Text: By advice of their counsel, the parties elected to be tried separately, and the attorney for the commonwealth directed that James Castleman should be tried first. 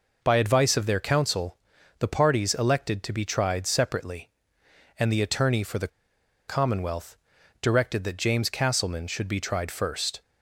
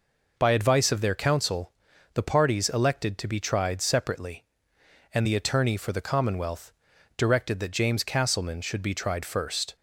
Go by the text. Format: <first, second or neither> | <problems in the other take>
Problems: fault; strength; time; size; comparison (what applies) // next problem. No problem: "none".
second | pauses between "the" and "commonwealth"; noticeable; at 5.8 s; 0.60 s long // pauses between "commonwealth" and "directed"; at 7.1 s; 0.44 s long; also in the second